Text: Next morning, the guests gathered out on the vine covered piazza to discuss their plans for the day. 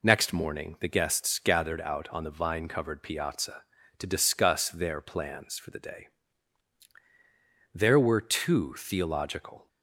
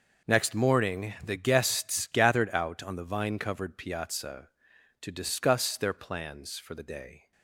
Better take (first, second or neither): second